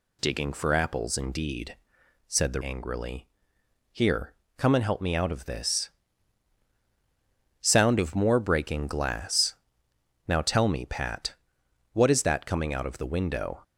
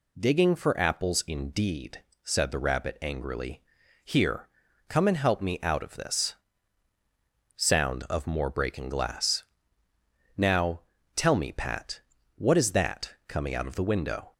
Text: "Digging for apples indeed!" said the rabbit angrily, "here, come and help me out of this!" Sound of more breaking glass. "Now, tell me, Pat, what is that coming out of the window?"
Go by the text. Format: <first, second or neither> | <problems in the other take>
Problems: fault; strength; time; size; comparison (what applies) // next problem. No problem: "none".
second | skips "rabbit"; at 2.6 s